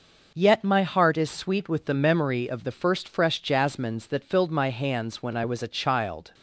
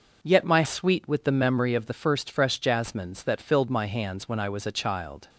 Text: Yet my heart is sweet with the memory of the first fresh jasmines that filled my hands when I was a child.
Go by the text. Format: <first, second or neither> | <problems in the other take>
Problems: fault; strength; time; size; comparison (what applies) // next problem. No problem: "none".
first | skips "heart is"; at 0.6 s